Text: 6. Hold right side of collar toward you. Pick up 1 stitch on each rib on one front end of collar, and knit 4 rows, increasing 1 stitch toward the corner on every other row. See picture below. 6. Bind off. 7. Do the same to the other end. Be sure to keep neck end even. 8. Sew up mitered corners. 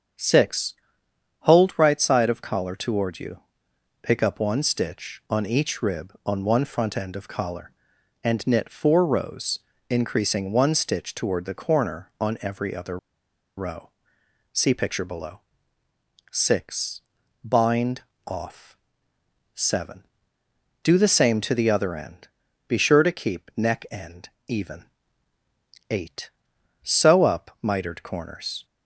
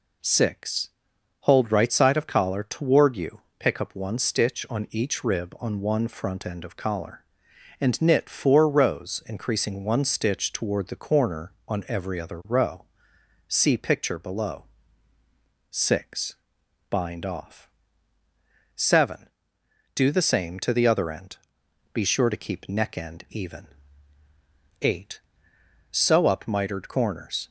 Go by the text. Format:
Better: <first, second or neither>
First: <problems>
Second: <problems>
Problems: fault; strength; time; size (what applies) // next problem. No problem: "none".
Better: second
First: starts louder than the rest; strong; until 1.8 s; 8 dB // pauses between "other" and "row"; noticeable; at 12.9 s; 0.60 s long // pauses between "Bind" and "off"; slight; at 18.0 s; 0.24 s long // pauses between "end" and "even"; slight; at 24.2 s; 0.18 s long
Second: none